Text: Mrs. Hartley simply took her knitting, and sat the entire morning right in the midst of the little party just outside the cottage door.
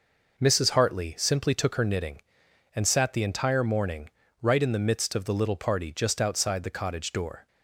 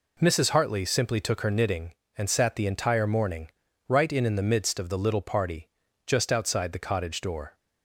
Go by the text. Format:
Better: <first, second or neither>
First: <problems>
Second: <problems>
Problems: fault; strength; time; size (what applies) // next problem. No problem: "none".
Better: first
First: pauses between "morning" and "right"; slight; at 4.1 s; 0.32 s long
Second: pauses between "morning" and "right"; at 3.4 s; 0.38 s long // says "in" twice; at 4.2 s // pauses between "party" and "just"; at 5.6 s; 0.38 s long